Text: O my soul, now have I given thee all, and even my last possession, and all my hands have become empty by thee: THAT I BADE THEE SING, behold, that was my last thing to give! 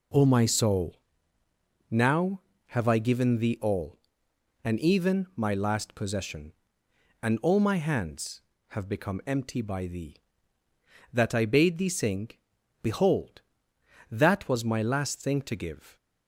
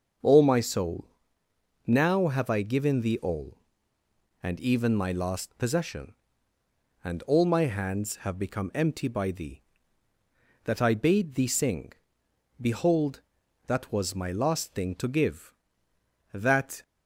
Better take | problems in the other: first | starts louder than the rest; until 2.0 s; 6.5 dB // goes on to say "That"; slight; from 16.3 s on; 0.48 s long

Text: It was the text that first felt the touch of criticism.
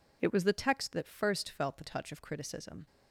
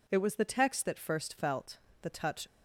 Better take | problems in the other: first | pauses between "felt" and "the"; slight; at 1.7 s; 0.22 s long // stops before "of criticism"; at 2.4 s

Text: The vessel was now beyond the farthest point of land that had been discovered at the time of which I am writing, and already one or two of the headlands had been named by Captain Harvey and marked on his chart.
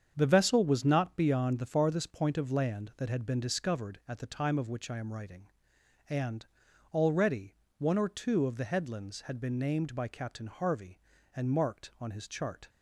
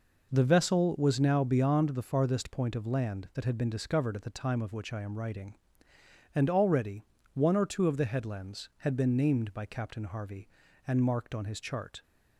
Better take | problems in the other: second | starts louder than the rest; strong; until 1.1 s; 7.5 dB // says "not" for "now"; at 0.8 s // pauses between "and" and "already"; noticeable; at 6.4 s; 0.46 s long // pauses between "already" and "one"; slight; at 7.5 s; 0.24 s long; slight in the second

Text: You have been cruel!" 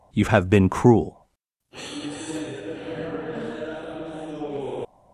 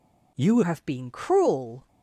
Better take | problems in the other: first | changes voice at "have"; from 0.6 s on; 1.2 s long

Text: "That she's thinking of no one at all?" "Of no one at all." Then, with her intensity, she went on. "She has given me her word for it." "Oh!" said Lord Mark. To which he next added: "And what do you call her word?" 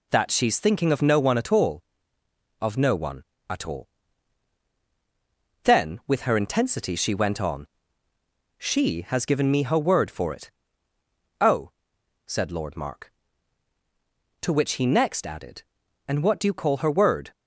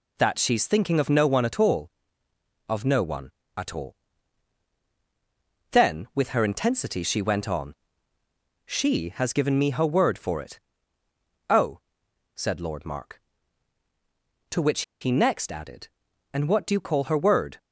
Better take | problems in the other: first | pauses between "which" and "he"; slight; at 14.8 s; 0.19 s long

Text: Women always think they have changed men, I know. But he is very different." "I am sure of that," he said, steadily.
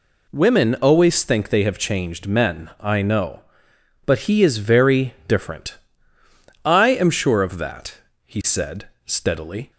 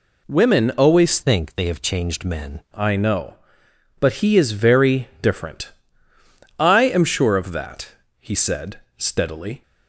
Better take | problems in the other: first | changes voice from "think" to "men"; from 1.2 to 2.6 s; 1.4 s long

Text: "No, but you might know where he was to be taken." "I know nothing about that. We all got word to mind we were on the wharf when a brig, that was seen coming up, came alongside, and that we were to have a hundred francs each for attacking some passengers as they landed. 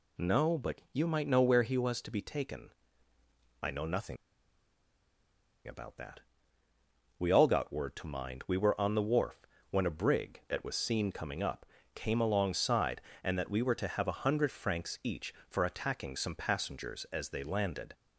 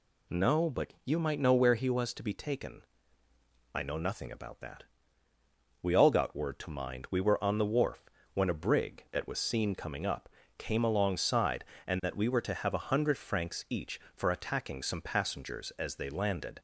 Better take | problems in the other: second | pauses between "nothing" and "about"; strong; at 4.1 s; 1.5 s long // pauses between "wharf" and "when"; slight; at 9.4 s; 0.24 s long; slight in the second

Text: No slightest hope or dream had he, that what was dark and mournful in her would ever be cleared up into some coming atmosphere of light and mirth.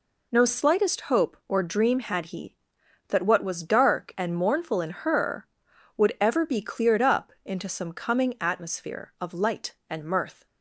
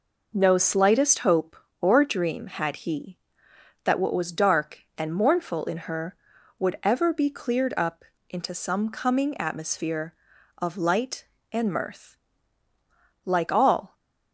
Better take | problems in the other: first | pauses between "up" and "into"; slight; at 8.0 s; 0.28 s long // goes on to say "Like all"; noticeable; from 13.2 s on; 0.68 s long

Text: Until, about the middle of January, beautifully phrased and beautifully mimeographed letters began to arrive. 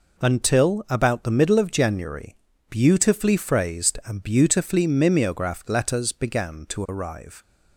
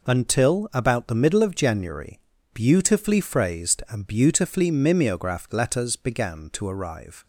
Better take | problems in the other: neither | none

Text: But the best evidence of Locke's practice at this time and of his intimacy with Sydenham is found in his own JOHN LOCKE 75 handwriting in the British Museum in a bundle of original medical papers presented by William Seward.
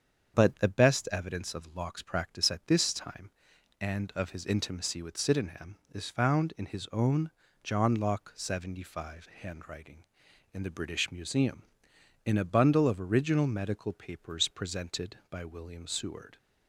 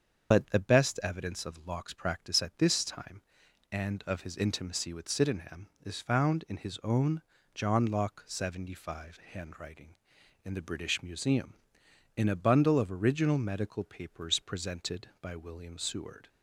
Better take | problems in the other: first | loses the start of "But"; at 0.3 s; 45 ms // starts louder than the rest; until 1.3 s; 7 dB; strong in the first // pauses between "own" and "JOHN"; slight; at 7.2 s; 0.32 s long; slight in the first

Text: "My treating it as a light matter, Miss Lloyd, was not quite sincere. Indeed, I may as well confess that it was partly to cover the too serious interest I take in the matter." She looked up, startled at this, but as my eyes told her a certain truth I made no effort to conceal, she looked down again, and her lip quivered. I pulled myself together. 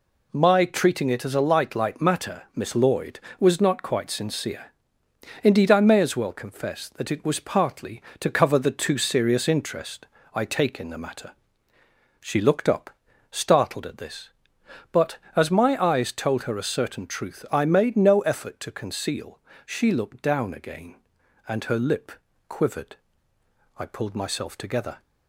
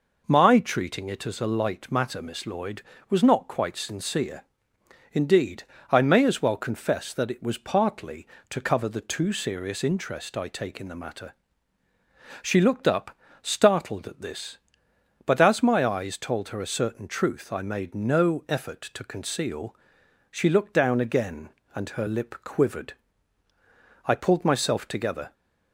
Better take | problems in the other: second | says "light" twice; at 1.7 s // pauses between "interest" and "I"; slight; at 10.0 s; 0.28 s long // pauses between "lip" and "quivered"; slight; at 22.1 s; 0.36 s long

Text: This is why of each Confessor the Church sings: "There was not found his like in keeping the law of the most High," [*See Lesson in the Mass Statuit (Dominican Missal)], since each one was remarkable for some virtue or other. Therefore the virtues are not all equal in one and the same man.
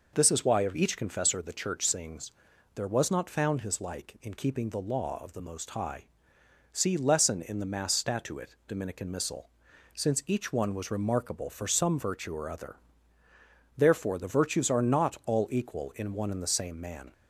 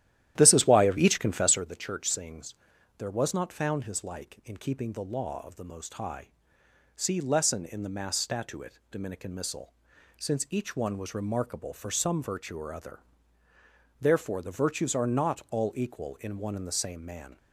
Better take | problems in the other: first | starts louder than the rest; strong; until 1.7 s; 12.5 dB

